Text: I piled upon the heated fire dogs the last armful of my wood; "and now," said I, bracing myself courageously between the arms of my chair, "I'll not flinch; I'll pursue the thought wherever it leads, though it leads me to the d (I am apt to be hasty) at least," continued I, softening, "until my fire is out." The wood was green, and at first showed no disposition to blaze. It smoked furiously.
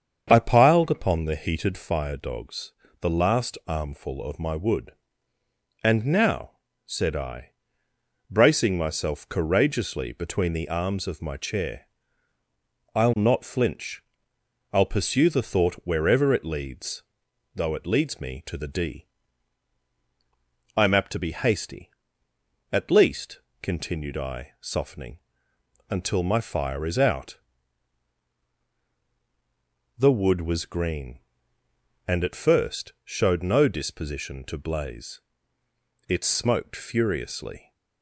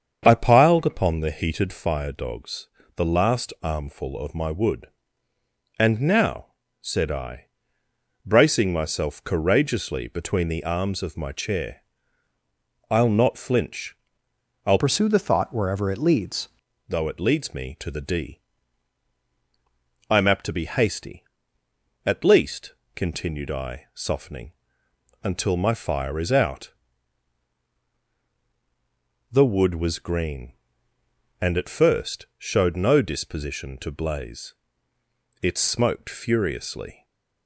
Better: first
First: starts louder than the rest; strong; until 1.3 s; 7 dB // pauses between "dogs" and "the"; slight; at 2.7 s; 0.28 s long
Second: starts louder than the rest; strong; until 1.2 s; 7 dB // pauses between "dogs" and "the"; slight; at 2.6 s; 0.28 s long // changes voice from "pursue" to "leads"; from 14.7 to 16.4 s; 1.7 s long // stays silent after the last word; slight; from 36.9 s on; 0.5 s long

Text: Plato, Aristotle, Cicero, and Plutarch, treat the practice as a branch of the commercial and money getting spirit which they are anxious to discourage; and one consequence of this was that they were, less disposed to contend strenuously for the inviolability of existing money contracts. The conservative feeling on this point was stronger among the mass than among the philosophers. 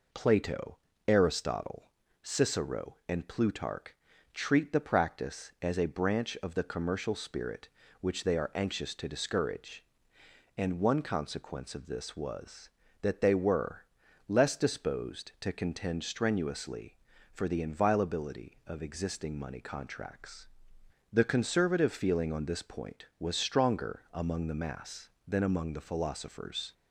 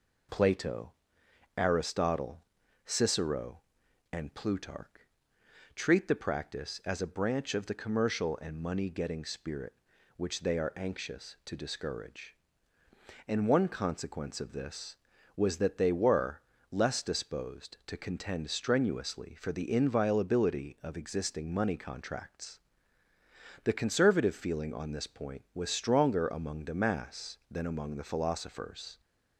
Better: second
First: skips "and money getting"; at 7.1 s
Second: none

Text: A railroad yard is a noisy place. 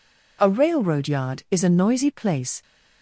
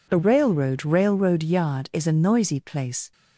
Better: first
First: none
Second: says "railroad" twice; at 0.8 s

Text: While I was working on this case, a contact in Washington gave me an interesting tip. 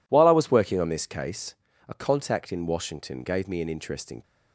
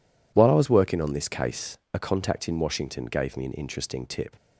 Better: second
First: stops before "tip"; at 4.2 s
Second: none

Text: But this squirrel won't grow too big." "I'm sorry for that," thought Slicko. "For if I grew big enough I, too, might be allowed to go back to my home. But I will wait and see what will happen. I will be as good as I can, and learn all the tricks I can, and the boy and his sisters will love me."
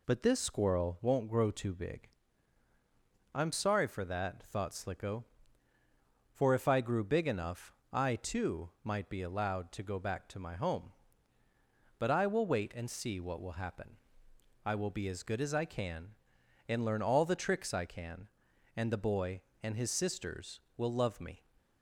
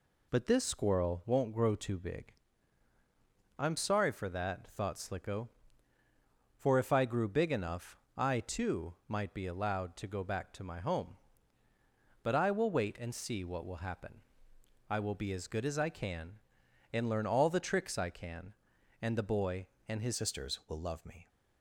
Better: first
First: pauses between "enough" and "I"; slight; at 7.7 s; 0.18 s long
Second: pauses between "enough" and "I"; slight; at 7.9 s; 0.18 s long // changes voice at "sisters"; from 20.1 s on; 1.1 s long

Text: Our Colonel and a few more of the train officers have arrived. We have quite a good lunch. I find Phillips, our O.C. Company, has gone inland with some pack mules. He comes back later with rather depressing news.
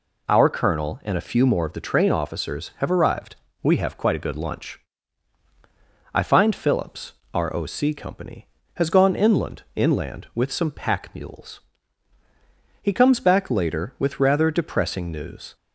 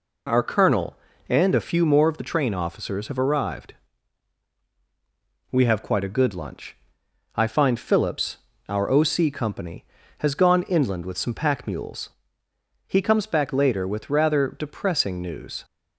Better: second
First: says "inland" twice; at 9.7 s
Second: none

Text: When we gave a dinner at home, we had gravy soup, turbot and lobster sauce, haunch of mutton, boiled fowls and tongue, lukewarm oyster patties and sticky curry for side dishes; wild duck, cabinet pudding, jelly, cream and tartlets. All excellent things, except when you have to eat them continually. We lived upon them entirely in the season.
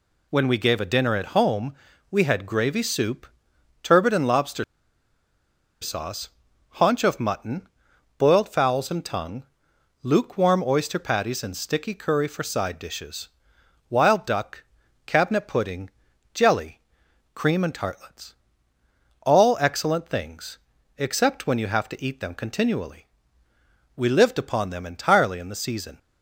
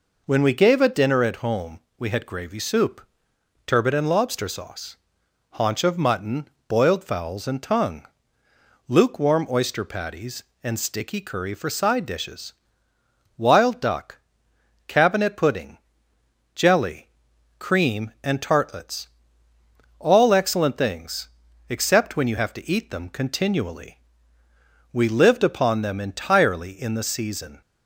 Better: second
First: pauses between "lobster" and "sauce"; at 4.6 s; 1.1 s long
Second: none

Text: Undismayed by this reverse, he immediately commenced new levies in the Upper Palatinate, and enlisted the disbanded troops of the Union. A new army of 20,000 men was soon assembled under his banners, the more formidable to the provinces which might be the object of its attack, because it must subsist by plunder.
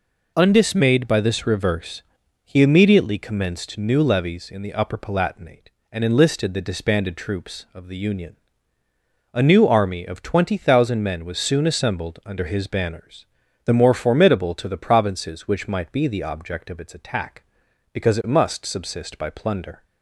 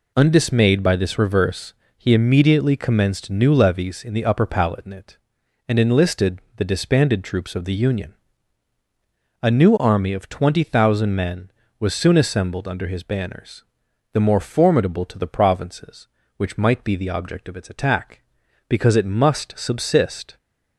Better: first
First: none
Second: pauses between "enlisted" and "the"; slight; at 6.3 s; 0.18 s long // stops before "by plunder"; at 20.3 s

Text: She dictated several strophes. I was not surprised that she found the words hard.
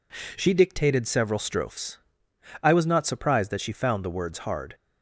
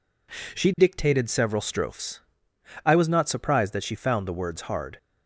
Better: neither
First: none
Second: none

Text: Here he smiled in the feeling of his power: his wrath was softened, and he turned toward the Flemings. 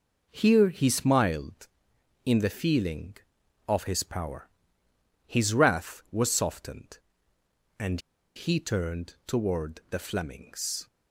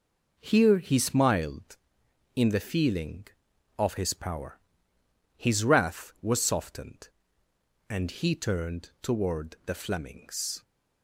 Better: second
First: pauses between "and" and "he"; at 7.9 s; 0.37 s long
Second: none

